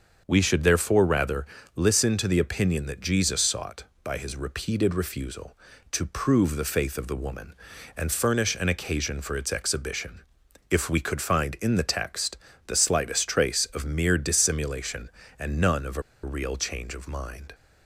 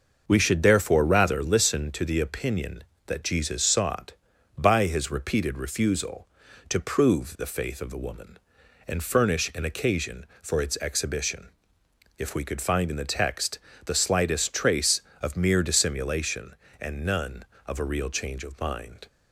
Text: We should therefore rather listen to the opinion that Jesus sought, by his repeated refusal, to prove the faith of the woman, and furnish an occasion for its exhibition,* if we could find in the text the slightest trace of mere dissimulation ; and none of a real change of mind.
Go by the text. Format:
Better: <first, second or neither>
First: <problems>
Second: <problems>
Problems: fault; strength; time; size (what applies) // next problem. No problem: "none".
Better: second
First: starts louder than the rest; until 1.2 s; 6.5 dB // pauses between "rather" and "listen"; slight; at 1.4 s; 0.30 s long // pauses between "text" and "the"; slight; at 12.3 s; 0.28 s long // pauses between "a" and "real"; slight; at 16.0 s; 0.21 s long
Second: starts louder than the rest; noticeable; until 1.2 s; 6 dB // pauses between "text" and "the"; slight; at 13.5 s; 0.28 s long